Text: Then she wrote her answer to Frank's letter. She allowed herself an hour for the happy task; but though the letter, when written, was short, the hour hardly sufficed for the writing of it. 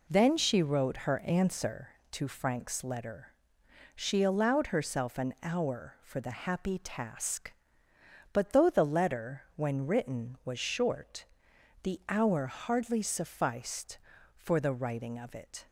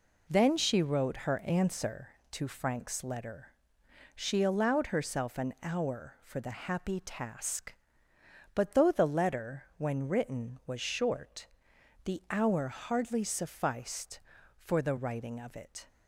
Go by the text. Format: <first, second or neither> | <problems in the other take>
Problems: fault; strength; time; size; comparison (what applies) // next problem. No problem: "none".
neither | none